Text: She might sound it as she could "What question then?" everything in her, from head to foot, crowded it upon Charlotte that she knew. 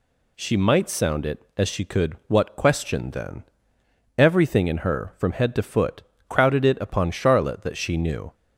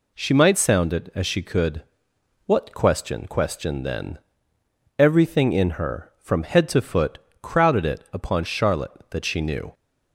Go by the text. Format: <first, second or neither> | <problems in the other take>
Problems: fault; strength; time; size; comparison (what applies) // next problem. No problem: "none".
first | pauses between "could" and "What"; noticeable; at 1.8 s; 0.64 s long // says "question" twice; at 3.2 s